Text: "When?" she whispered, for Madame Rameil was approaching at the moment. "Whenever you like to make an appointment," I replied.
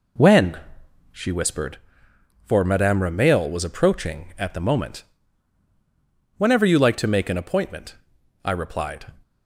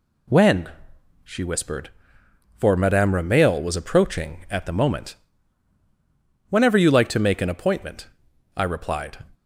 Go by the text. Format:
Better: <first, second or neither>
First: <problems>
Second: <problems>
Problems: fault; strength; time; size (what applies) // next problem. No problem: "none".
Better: second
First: starts louder than the rest; until 1.9 s; 4 dB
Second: none